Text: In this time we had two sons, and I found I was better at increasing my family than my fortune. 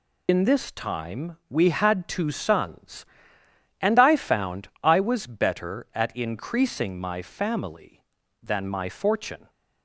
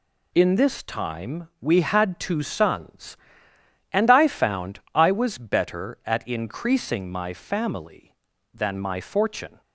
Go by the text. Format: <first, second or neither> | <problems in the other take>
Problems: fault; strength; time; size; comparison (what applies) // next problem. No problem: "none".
second | loses the start of "In"; at 0.2 s; 75 ms // pauses between "found" and "I"; slight; at 4.6 s; 0.16 s long; slight in the second